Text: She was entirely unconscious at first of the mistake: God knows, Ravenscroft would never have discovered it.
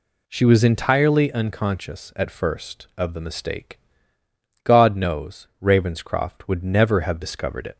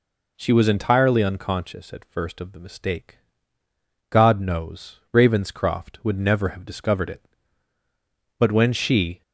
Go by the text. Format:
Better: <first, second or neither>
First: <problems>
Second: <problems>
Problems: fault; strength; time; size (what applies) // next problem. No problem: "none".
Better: first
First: none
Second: goes on to say "But when she"; noticeable; from 8.3 s on; 0.84 s long